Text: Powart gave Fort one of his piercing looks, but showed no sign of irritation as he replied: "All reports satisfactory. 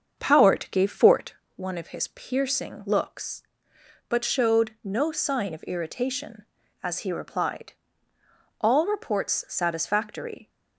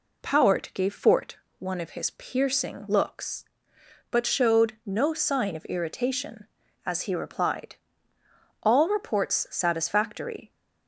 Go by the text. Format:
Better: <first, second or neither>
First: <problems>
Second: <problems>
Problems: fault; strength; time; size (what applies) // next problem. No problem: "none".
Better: second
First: starts louder than the rest; strong; until 1.5 s; 7 dB // pauses between "Fort" and "one"; slight; at 1.3 s; 0.22 s long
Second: pauses between "Fort" and "one"; slight; at 1.3 s; 0.22 s long